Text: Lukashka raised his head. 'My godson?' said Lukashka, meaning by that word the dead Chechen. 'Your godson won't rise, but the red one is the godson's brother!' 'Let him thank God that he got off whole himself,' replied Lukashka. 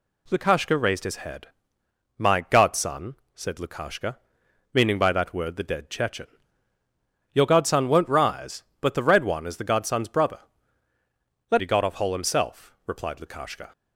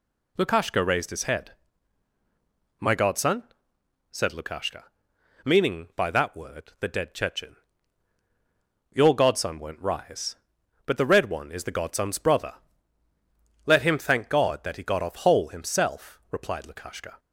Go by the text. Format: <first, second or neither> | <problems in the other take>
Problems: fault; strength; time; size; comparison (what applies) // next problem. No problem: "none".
second | skips "him thank God that"; at 11.6 s